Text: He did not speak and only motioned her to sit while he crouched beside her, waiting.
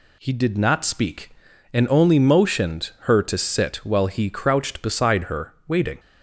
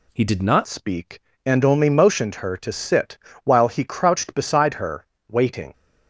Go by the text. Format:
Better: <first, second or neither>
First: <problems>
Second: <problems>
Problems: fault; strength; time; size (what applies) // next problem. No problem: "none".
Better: first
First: none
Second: changes voice at "speak"; from 0.6 s on; 5.1 s long // pauses between "sit" and "while"; slight; at 3.1 s; 0.28 s long